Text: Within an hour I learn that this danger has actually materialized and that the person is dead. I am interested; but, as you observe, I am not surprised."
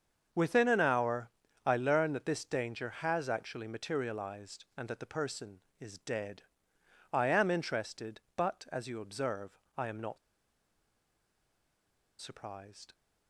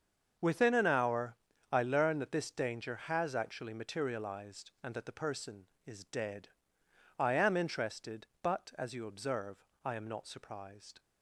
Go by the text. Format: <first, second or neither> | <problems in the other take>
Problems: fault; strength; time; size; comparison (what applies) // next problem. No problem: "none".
second | starts louder than the rest; until 1.7 s; 7 dB; also in the second // pauses between "hour" and "I"; slight; at 1.2 s; 0.36 s long; slight in the second // pauses between "not" and "surprised"; strong; at 10.1 s; 2.0 s long